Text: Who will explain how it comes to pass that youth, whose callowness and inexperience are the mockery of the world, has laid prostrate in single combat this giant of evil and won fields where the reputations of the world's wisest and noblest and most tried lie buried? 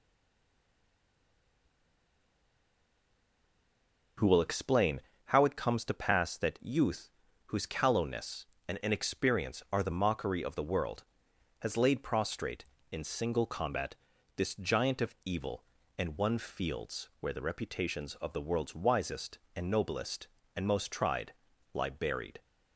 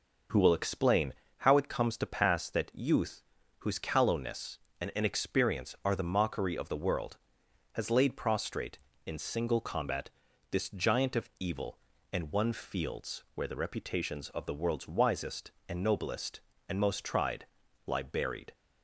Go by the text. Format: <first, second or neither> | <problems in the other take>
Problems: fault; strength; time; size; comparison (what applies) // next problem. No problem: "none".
second | stays silent before the first word; strong; until 4.1 s; 4.1 s long // starts louder than the rest; noticeable; until 5.4 s; 6 dB // pauses between "explain" and "how"; slight; at 5.0 s; 0.26 s long; slight in the second // pauses between "combat" and "this"; at 13.9 s; 0.42 s long; also in the second // pauses between "tried" and "lie"; at 21.3 s; 0.40 s long; also in the second